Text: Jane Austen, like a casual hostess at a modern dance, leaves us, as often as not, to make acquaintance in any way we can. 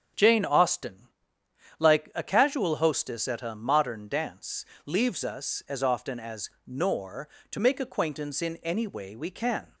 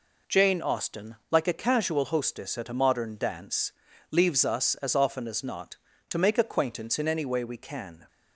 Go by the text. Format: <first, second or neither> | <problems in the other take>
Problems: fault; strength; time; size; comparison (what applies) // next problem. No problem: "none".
second | starts louder than the rest; strong; until 1.8 s; 7 dB // says "nor" for "not"; at 6.6 s